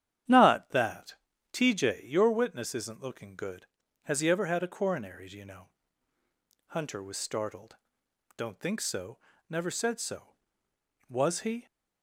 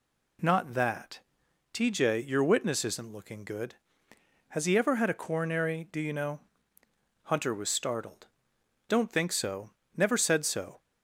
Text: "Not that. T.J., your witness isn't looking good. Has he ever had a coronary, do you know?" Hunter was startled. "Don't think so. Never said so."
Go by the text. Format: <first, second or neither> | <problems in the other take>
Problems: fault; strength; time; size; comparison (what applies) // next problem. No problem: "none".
second | starts louder than the rest; strong; until 1.6 s; 10 dB // goes on to say "Was he"; from 11.0 s on; 0.56 s long